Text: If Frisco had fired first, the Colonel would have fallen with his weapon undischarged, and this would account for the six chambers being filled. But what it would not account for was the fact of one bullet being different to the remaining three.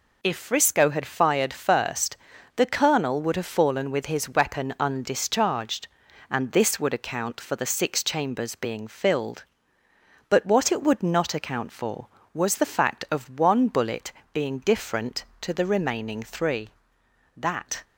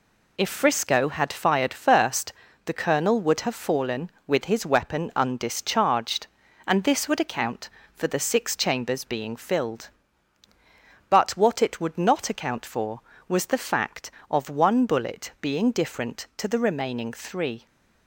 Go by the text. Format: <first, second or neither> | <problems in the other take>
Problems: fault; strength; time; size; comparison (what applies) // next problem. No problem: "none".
second | pauses between "bullet" and "being"; slight; at 14.1 s; 0.20 s long // goes on to say "That"; slight; from 17.3 s on; 0.48 s long